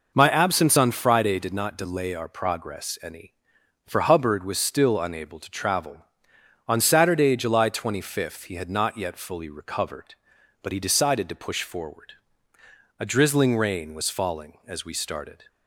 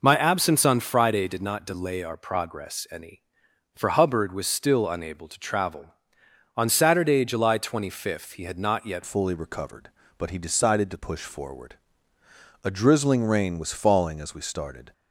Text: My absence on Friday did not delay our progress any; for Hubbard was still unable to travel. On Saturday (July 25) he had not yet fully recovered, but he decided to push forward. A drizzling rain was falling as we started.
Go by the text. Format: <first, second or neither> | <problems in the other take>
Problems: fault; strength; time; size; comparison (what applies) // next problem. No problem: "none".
first | changes voice at "fully"; from 9.0 s on; 5.9 s long